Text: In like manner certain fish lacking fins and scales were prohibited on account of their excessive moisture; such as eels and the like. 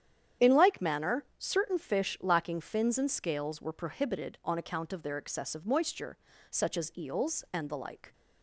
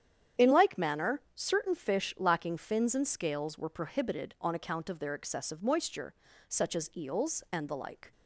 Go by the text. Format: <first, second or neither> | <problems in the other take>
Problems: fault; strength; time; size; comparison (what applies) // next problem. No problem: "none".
neither | starts louder than the rest; strong; the same in both